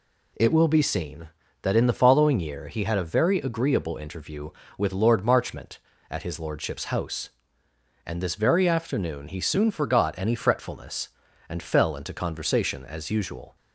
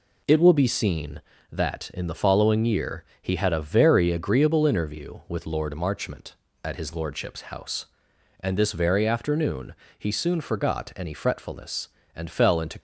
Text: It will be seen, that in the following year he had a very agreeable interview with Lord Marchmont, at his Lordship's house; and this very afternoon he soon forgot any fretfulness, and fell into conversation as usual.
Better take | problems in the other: first | pauses between "year" and "he"; slight; at 3.0 s; 0.18 s long // pauses between "afternoon" and "he"; slight; at 9.7 s; 0.26 s long // stops before "conversation as usual"; at 12.7 s

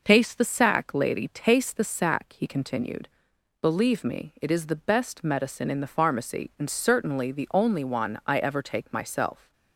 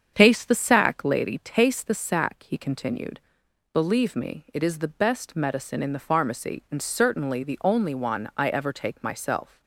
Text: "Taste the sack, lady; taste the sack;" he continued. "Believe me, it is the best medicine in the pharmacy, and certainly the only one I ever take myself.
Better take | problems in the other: first | starts louder than the rest; strong; until 1.2 s; 7.5 dB

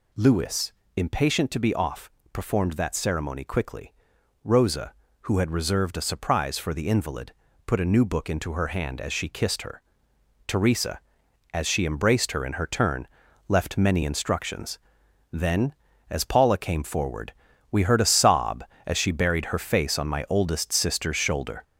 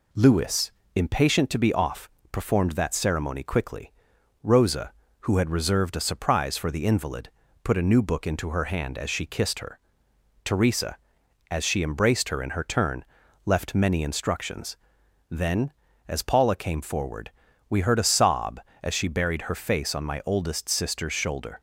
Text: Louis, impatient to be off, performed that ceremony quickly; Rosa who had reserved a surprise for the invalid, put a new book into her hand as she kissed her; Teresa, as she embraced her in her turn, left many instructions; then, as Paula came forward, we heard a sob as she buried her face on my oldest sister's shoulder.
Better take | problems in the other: second | gets louder; noticeable; throughout; 5 dB

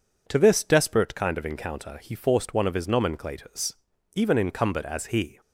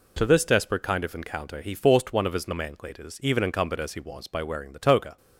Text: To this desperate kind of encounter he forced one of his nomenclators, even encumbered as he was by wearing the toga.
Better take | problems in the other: second | stops before "was by wearing the toga"; at 5.4 s

